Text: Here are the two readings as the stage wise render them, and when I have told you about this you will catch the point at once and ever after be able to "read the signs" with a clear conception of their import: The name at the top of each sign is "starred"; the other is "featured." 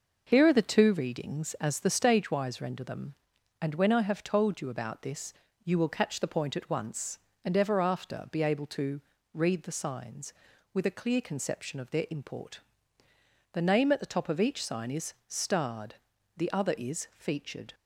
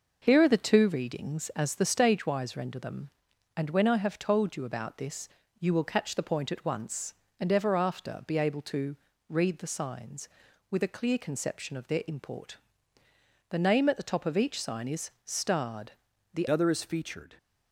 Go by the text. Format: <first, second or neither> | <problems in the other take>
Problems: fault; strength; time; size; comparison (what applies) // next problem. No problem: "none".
first | pauses between "this" and "you"; slight; at 5.2 s; 0.32 s long; slight in the first // pauses between "to" and "read"; slight; at 8.9 s; 0.32 s long; slight in the first // changes voice at "other"; from 16.5 s on; 0.8 s long